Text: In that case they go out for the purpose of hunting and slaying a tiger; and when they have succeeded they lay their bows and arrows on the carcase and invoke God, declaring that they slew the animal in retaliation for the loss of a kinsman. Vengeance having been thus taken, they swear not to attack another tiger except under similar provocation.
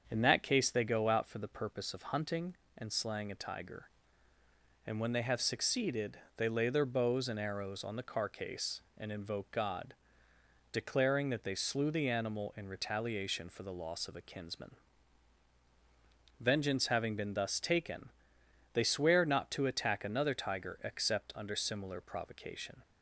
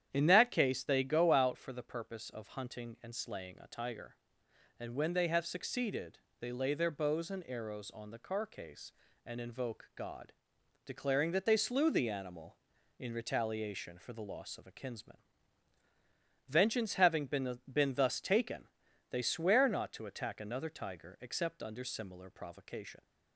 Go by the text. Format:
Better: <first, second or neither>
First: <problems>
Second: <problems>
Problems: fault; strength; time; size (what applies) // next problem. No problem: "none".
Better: first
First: starts louder than the rest; until 1.1 s; 7 dB // pauses between "succeeded" and "they"; slight; at 6.1 s; 0.18 s long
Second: starts louder than the rest; strong; until 1.1 s; 9.5 dB // pauses between "succeeded" and "they"; slight; at 6.1 s; 0.22 s long // says "been" twice; at 17.7 s